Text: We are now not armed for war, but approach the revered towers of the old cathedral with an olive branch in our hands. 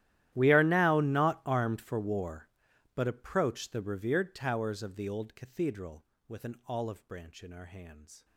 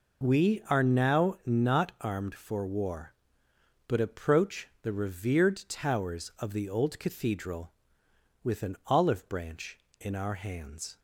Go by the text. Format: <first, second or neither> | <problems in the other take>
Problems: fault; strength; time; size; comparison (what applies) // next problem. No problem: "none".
second | gets quieter; strong; throughout; 25 dB